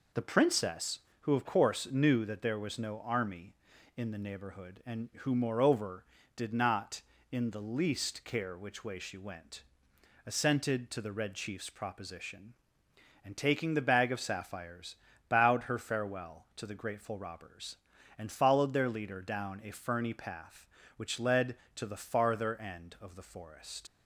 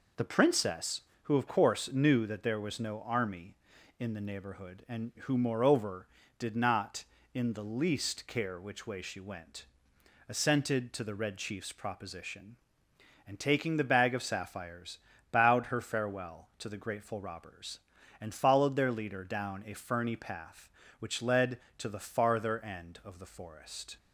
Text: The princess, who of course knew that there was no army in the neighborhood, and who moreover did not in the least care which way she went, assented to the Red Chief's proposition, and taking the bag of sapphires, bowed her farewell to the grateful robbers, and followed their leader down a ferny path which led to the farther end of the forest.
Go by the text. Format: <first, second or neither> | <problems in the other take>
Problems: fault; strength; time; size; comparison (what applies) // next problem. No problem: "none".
second | leaves "forest" unfinished; at 23.8 s; 60 ms